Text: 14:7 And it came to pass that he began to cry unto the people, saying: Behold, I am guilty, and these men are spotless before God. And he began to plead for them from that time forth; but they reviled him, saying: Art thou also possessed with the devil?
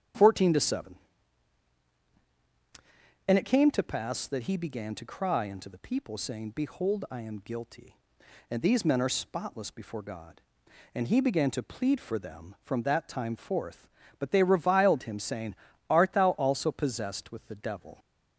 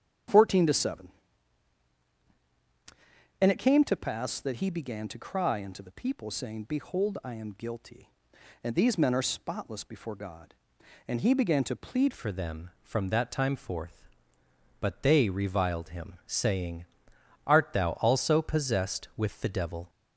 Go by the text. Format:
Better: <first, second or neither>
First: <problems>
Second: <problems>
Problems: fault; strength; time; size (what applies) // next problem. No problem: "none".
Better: first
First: starts louder than the rest; strong; until 3.4 s; 9 dB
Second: starts louder than the rest; strong; until 3.6 s; 9 dB // changes voice at "for"; from 12.1 s on; 7.7 s long